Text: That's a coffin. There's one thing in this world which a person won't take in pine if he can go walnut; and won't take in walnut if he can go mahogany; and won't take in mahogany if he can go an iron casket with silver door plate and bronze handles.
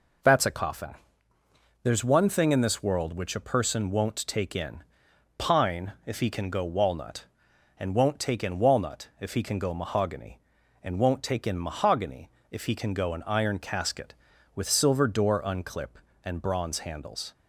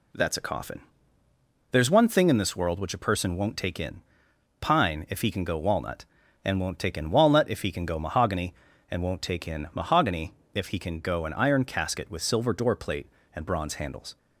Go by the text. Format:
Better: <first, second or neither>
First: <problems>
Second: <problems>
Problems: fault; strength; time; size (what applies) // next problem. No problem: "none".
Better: second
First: pauses between "in" and "pine"; noticeable; at 4.8 s; 0.56 s long // pauses between "mahogany" and "if"; slight; at 12.2 s; 0.22 s long // says "unclip" for "plate"; at 15.4 s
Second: pauses between "in" and "pine"; noticeable; at 4.0 s; 0.58 s long // pauses between "mahogany" and "if"; slight; at 10.3 s; 0.20 s long